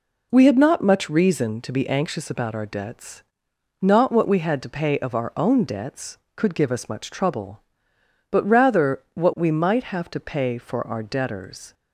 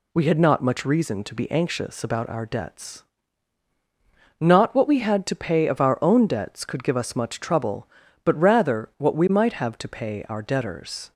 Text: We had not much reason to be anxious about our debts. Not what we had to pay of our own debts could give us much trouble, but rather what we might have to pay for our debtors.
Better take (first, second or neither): first